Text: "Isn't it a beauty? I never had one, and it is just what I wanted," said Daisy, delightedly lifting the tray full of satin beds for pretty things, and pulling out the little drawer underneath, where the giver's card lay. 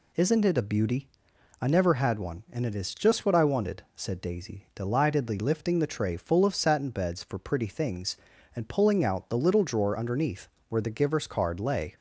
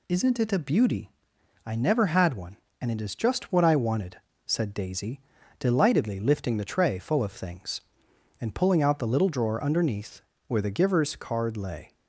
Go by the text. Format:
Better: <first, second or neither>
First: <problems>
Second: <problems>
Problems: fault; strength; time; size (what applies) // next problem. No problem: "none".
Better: first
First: none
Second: skips "satin beds for pretty"; at 7.3 s